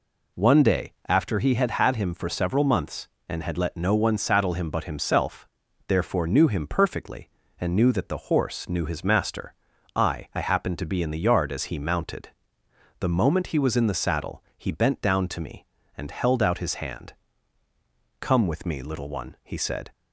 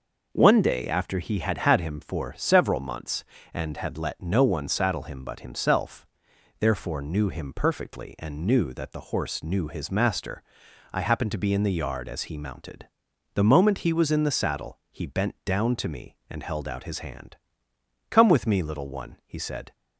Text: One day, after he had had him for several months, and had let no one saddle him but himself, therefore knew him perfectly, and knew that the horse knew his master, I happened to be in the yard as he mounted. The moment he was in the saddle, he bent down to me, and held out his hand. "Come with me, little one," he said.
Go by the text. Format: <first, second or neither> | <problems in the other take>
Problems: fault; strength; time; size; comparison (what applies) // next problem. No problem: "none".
second | says "I" twice; at 10.3 s